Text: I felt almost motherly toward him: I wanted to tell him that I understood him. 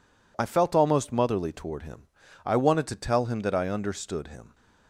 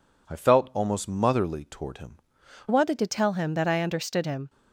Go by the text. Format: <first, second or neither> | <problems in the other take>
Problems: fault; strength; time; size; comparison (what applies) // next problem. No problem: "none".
first | changes voice at "wanted"; from 2.6 s on; 1.8 s long